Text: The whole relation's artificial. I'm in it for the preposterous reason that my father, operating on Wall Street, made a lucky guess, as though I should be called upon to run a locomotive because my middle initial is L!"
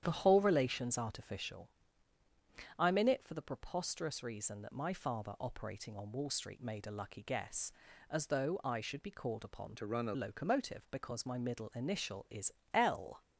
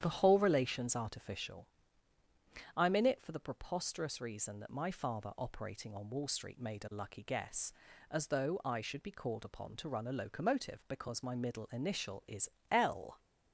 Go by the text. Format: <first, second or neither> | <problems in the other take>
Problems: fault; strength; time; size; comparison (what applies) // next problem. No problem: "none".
second | starts louder than the rest; strong; until 1.0 s; 9.5 dB; strong in the second // changes voice from "to" to "a"; from 9.7 to 10.1 s; 0.4 s long // pauses between "is" and "L"; slight; at 12.5 s; 0.20 s long; slight in the second